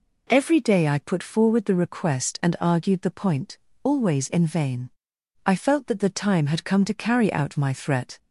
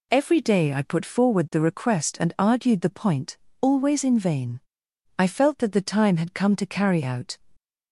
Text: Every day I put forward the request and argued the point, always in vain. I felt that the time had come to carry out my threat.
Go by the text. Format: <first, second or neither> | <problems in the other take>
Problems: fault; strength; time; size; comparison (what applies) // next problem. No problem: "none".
first | stops before "my threat"; at 7.5 s